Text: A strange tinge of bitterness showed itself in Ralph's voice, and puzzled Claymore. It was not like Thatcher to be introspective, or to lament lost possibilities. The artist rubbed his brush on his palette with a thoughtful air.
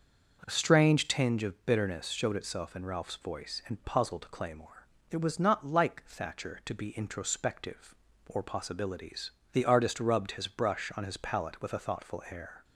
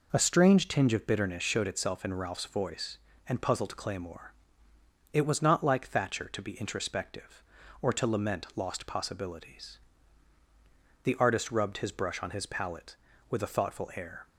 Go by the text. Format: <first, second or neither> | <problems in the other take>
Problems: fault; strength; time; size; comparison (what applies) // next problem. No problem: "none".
second | starts louder than the rest; until 1.4 s; 6.5 dB // skips "to lament lost"; at 8.4 s